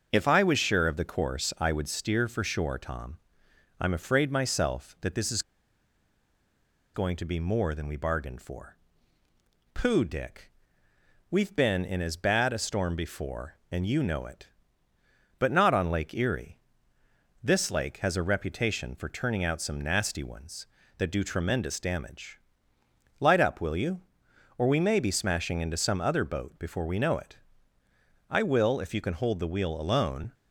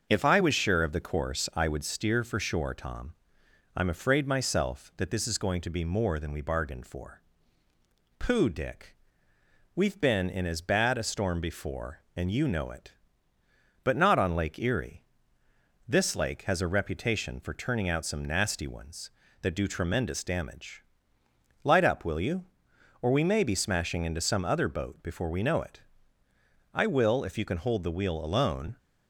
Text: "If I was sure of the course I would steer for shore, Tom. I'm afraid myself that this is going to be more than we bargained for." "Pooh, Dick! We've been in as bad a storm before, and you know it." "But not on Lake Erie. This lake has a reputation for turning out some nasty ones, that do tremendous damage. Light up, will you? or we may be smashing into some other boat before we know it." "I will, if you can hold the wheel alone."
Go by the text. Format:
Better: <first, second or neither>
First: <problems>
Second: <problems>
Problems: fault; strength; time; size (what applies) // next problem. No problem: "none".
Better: second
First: starts louder than the rest; until 1.1 s; 6.5 dB // pauses between "is" and "going"; strong; at 5.4 s; 1.5 s long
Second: starts louder than the rest; until 1.1 s; 6.5 dB